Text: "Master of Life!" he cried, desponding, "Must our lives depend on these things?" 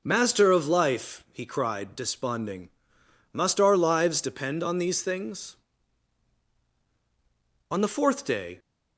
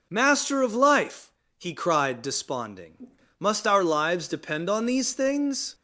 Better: second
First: goes on to say "On the fourth day"; noticeable; from 7.7 s on; 0.88 s long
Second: none

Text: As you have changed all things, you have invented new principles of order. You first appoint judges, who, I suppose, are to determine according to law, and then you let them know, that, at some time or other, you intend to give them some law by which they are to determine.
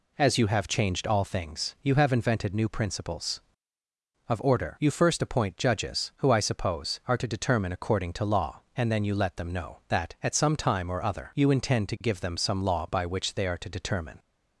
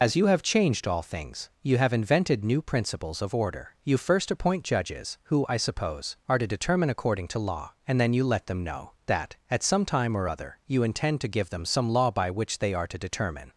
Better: first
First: none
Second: loses the start of "As"; at 0.0 s; 110 ms

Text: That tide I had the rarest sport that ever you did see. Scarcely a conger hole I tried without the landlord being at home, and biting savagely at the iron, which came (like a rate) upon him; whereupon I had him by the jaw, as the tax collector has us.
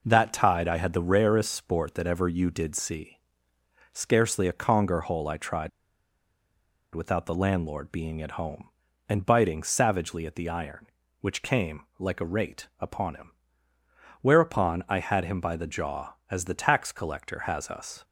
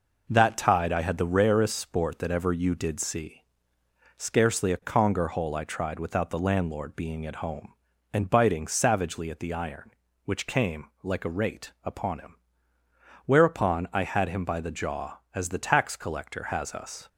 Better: second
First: pauses between "tried" and "without"; strong; at 5.6 s; 1.2 s long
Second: none

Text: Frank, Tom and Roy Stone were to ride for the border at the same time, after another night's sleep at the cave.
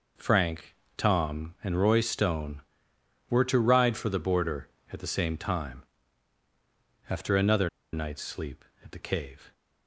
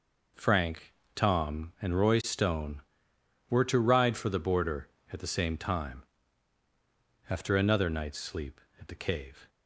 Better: second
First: pauses between "another" and "night's"; slight; at 7.6 s; 0.24 s long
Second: none

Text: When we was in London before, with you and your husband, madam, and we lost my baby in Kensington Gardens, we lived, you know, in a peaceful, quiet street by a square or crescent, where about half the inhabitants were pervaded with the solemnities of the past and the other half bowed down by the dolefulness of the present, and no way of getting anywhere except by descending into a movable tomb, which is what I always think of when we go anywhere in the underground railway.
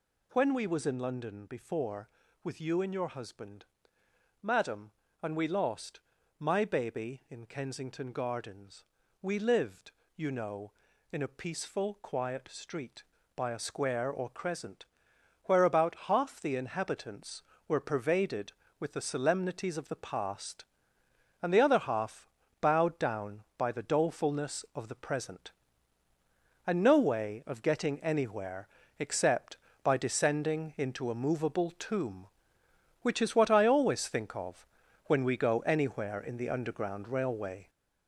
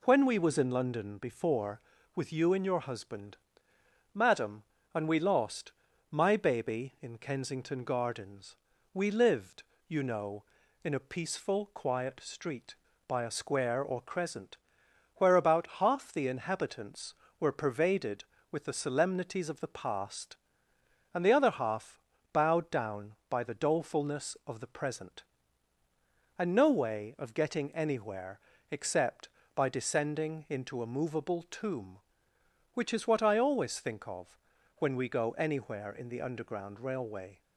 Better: second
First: gets louder; throughout; 6.5 dB // pauses between "lost" and "my"; slight; at 6.0 s; 0.36 s long // pauses between "half" and "bowed"; slight; at 22.2 s; 0.34 s long // pauses between "anywhere" and "except"; slight; at 28.6 s; 0.32 s long // pauses between "of" and "when"; noticeable; at 34.5 s; 0.50 s long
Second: pauses between "lost" and "my"; slight; at 5.7 s; 0.36 s long // pauses between "half" and "bowed"; slight; at 21.9 s; 0.34 s long // pauses between "anywhere" and "except"; slight; at 28.3 s; 0.32 s long // pauses between "of" and "when"; noticeable; at 34.2 s; 0.50 s long

